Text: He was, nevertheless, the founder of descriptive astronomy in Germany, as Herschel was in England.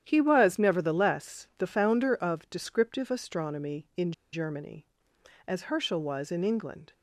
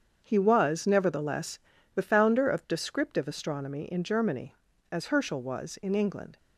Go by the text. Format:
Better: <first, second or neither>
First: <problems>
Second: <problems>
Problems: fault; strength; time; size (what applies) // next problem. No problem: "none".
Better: second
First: starts louder than the rest; strong; until 1.0 s; 10.5 dB // pauses between "in" and "Germany"; slight; at 4.1 s; 0.20 s long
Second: starts louder than the rest; strong; until 1.2 s; 7.5 dB